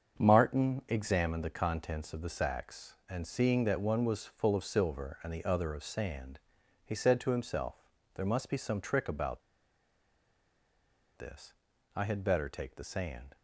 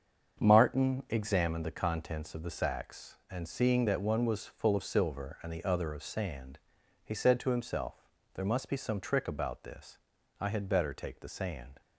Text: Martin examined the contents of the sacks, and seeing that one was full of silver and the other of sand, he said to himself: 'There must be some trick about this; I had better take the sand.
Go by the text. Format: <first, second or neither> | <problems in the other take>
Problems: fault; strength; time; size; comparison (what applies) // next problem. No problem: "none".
second | starts louder than the rest; until 1.2 s; 7 dB; also in the second // pauses between "about" and "this"; strong; at 9.4 s; 1.7 s long